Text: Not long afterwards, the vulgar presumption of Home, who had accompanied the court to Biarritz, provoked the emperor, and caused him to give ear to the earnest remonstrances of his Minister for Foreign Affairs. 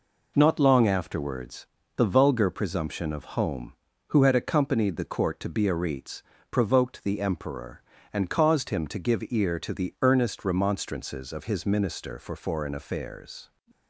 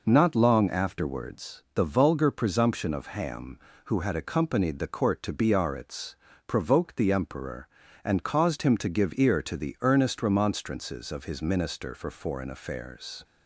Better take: first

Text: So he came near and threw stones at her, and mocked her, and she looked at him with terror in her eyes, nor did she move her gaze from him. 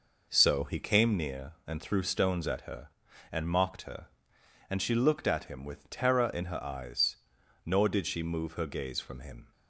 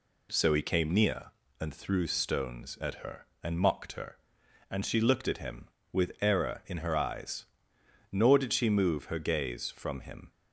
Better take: first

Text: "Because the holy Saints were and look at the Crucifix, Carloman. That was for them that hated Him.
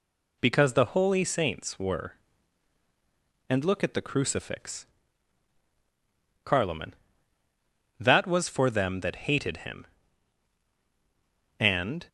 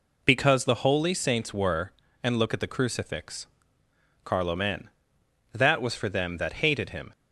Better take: second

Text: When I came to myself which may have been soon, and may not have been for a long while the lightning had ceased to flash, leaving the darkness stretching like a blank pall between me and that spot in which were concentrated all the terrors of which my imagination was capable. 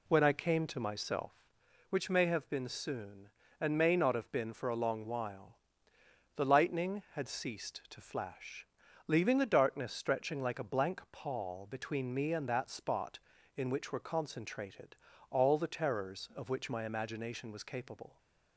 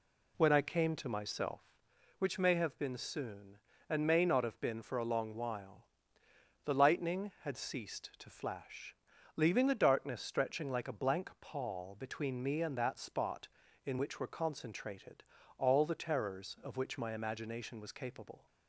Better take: neither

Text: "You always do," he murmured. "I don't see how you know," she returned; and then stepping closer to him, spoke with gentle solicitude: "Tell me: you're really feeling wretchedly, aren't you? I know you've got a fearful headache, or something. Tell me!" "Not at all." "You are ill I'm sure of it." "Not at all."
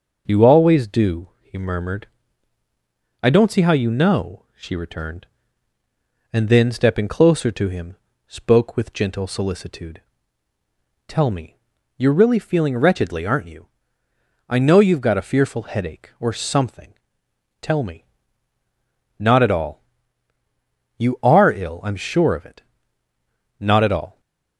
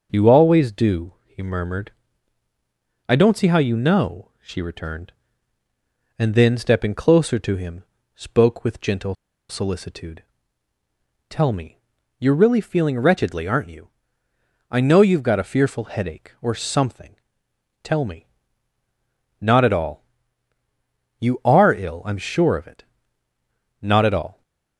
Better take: first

